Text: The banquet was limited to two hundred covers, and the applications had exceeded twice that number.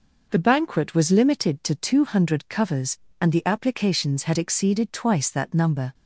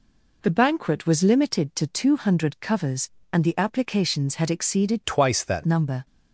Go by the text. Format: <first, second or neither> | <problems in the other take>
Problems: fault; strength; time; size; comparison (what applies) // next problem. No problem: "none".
first | changes voice from "twice" to "that"; from 5.0 to 5.6 s; 0.6 s long